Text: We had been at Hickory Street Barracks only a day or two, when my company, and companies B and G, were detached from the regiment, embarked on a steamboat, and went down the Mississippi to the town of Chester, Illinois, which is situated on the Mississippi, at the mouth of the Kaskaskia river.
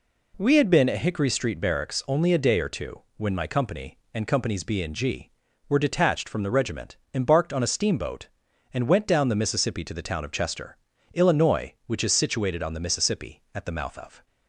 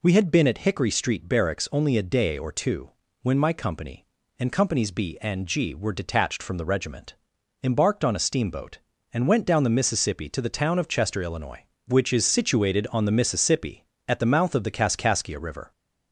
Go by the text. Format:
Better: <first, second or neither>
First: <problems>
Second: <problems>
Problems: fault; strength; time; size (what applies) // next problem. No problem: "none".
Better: second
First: stops before "the Kaskaskia river"; at 14.2 s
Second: none